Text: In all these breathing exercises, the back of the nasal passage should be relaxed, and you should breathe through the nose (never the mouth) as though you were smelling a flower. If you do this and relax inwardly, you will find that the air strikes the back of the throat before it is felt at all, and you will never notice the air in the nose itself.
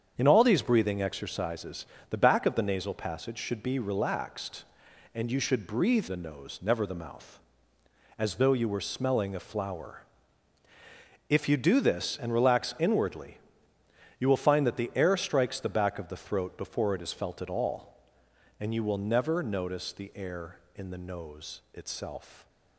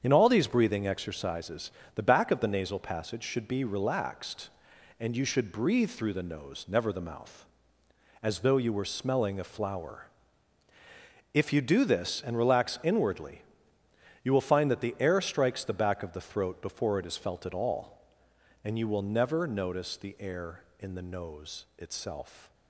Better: second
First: starts louder than the rest; strong; until 1.1 s; 7.5 dB // skips "through"; at 6.0 s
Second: starts louder than the rest; strong; until 1.0 s; 8 dB

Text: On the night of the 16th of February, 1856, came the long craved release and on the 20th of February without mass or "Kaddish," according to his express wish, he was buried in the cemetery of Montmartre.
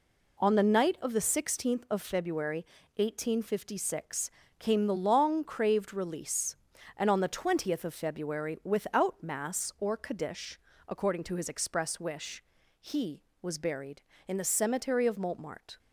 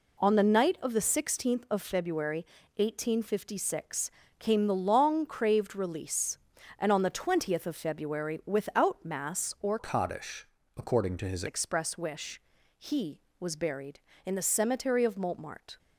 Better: first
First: none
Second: changes voice from "Kaddish" to "his"; from 9.7 to 11.4 s; 1.7 s long

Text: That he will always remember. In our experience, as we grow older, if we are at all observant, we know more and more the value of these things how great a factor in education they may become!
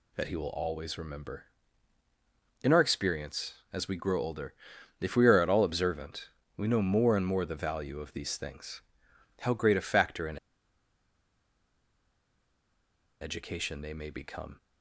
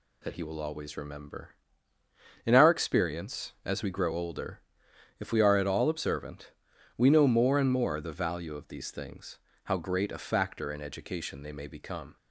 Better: second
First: pauses between "things" and "how"; noticeable; at 8.8 s; 0.60 s long // pauses between "in" and "education"; strong; at 10.3 s; 2.8 s long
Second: pauses between "things" and "how"; slight; at 9.3 s; 0.26 s long

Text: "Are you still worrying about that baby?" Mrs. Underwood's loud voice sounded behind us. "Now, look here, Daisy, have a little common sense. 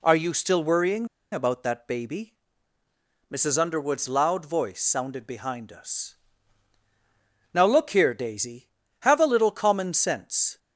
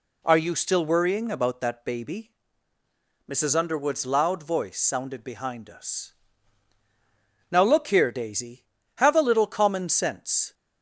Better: second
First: pauses between "worrying" and "about"; slight; at 1.0 s; 0.26 s long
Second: none

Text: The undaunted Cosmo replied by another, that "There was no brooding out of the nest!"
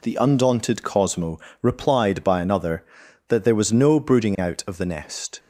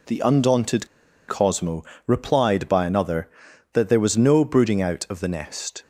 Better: first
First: pauses between "Cosmo" and "replied"; slight; at 1.3 s; 0.22 s long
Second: pauses between "undaunted" and "Cosmo"; at 0.8 s; 0.40 s long // pauses between "Cosmo" and "replied"; slight; at 1.8 s; 0.22 s long

